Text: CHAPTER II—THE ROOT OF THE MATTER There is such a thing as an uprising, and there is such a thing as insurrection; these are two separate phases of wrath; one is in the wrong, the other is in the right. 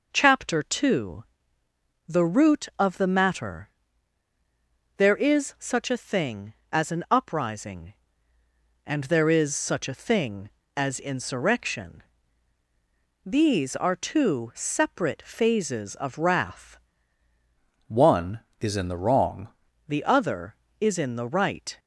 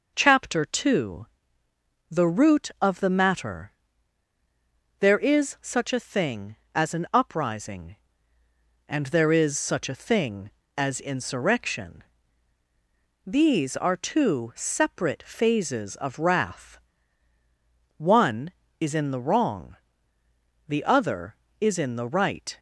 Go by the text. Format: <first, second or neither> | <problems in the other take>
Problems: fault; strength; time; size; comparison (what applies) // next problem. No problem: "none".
second | pauses between "MATTER" and "There"; strong; at 3.7 s; 1.2 s long; strong in the second // changes voice from "one" to "wrong"; from 17.8 to 19.4 s; 1.6 s long